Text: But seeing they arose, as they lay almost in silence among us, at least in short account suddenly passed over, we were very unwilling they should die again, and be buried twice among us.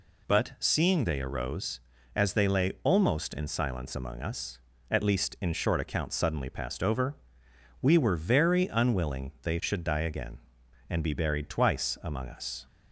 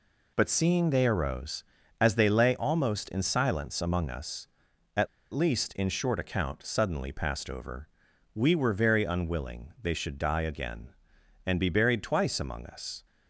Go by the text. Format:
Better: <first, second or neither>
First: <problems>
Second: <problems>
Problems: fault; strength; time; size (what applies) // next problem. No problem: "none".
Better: first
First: none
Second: pauses between "at" and "least"; slight; at 5.0 s; 0.25 s long